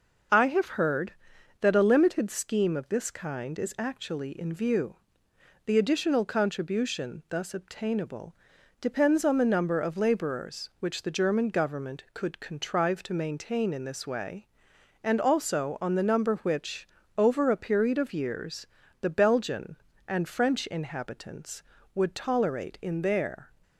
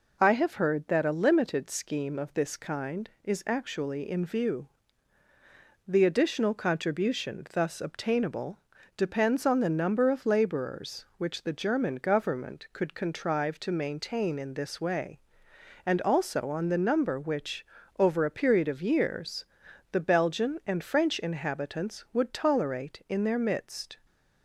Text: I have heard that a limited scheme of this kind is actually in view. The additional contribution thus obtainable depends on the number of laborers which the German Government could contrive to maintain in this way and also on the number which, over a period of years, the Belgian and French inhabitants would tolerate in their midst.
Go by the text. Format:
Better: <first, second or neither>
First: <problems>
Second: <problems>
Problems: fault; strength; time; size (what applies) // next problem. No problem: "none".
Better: second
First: pauses between "obtainable" and "depends"; at 8.3 s; 0.44 s long // stops before "midst"; at 23.6 s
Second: pauses between "obtainable" and "depends"; at 8.5 s; 0.38 s long